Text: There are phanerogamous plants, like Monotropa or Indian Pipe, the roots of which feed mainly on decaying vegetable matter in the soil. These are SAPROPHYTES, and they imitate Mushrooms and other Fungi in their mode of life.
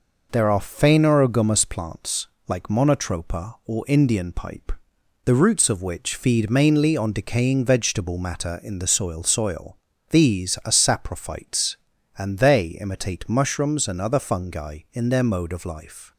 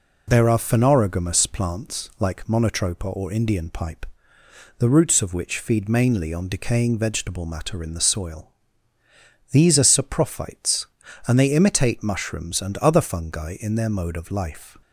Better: second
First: says "soil" twice; at 9.2 s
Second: none

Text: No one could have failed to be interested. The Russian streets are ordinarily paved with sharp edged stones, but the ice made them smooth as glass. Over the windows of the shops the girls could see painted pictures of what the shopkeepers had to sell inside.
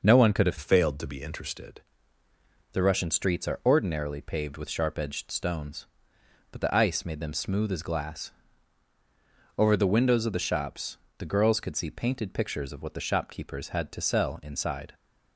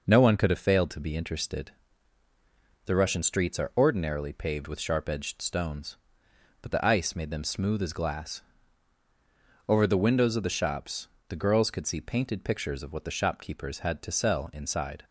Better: second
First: changes voice from "failed" to "interested"; from 0.5 to 1.8 s; 1.3 s long // pauses between "shops" and "the"; slight; at 10.9 s; 0.22 s long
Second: pauses between "shops" and "the"; slight; at 11.0 s; 0.22 s long

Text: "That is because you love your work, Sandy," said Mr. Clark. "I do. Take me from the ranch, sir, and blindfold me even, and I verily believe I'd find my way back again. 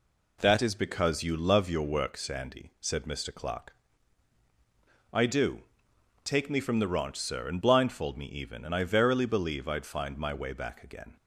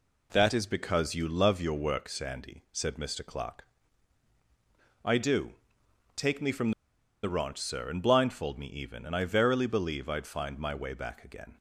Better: first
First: none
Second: pauses between "from" and "the"; noticeable; at 6.7 s; 0.52 s long

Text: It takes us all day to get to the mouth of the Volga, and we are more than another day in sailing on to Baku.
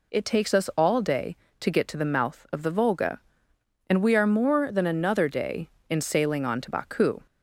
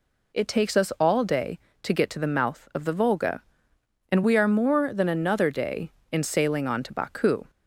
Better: neither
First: none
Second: none

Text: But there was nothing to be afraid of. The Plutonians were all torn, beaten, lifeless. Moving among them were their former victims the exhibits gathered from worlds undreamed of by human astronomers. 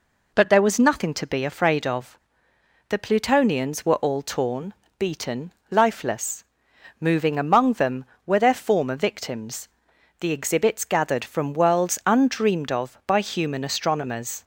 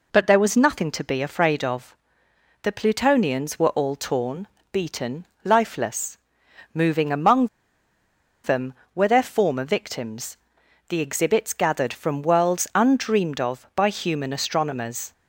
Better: first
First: pauses between "victims" and "the"; noticeable; at 9.6 s; 0.52 s long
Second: pauses between "among" and "them"; noticeable; at 7.4 s; 0.96 s long // pauses between "victims" and "the"; noticeable; at 10.3 s; 0.52 s long

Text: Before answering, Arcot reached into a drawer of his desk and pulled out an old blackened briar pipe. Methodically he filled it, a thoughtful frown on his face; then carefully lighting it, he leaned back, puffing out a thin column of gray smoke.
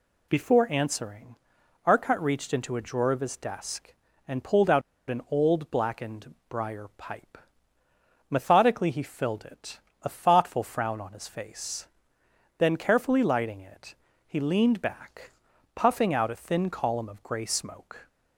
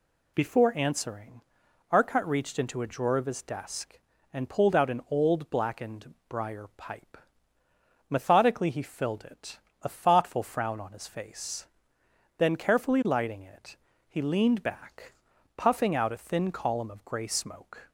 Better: second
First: pauses between "out" and "an"; slight; at 4.8 s; 0.27 s long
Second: none

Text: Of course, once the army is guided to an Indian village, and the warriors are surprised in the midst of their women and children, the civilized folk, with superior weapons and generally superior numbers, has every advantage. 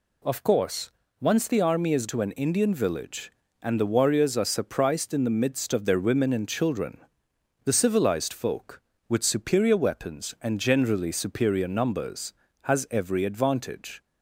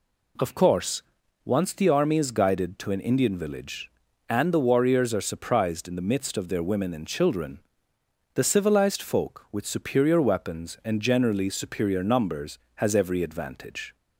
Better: second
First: skips "guided"; at 2.0 s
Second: none

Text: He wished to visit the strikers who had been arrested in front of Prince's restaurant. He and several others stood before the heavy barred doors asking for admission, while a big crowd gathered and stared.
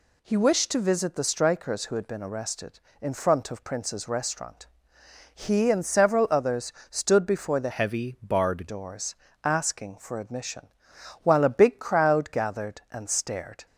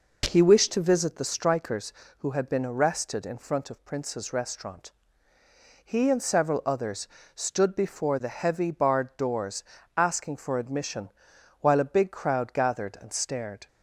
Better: second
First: pauses between "others" and "stood"; slight; at 6.7 s; 0.18 s long // changes voice from "heavy" to "barred"; from 7.7 to 8.6 s; 0.9 s long // pauses between "doors" and "asking"; slight; at 9.1 s; 0.28 s long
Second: pauses between "others" and "stood"; slight; at 7.0 s; 0.28 s long // pauses between "doors" and "asking"; slight; at 9.6 s; 0.32 s long

